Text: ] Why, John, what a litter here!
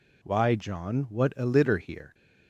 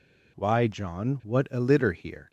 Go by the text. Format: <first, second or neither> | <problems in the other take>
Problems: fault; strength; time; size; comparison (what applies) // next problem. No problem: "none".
neither | none